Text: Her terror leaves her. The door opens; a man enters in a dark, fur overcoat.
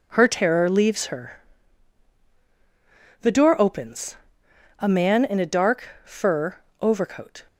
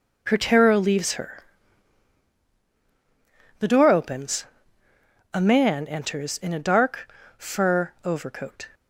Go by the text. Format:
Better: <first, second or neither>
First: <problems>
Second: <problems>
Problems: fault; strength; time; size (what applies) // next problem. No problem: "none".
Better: second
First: skips "enters"; at 5.2 s // pauses between "fur" and "overcoat"; slight; at 6.5 s; 0.24 s long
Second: none